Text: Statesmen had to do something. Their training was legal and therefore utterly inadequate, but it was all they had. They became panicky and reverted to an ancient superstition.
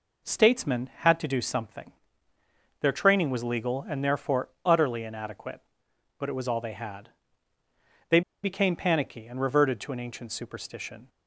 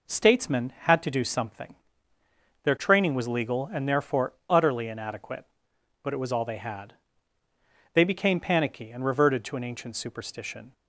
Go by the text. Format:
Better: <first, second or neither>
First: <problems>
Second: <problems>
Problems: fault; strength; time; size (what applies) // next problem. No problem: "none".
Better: second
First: pauses between "They" and "became"; slight; at 8.2 s; 0.22 s long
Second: none